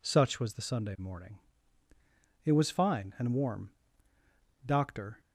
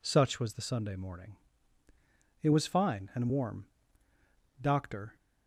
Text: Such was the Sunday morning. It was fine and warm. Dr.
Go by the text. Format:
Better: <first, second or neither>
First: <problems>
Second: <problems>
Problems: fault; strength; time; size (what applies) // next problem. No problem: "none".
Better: neither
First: none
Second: none